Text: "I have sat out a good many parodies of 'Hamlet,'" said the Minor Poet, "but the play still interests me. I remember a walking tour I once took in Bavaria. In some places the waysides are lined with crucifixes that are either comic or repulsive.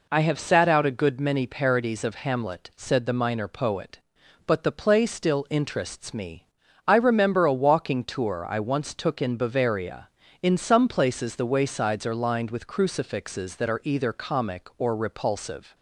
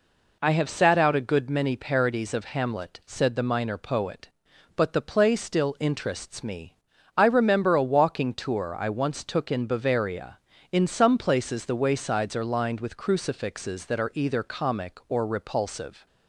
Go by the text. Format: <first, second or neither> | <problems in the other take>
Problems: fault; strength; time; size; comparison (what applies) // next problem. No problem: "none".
neither | none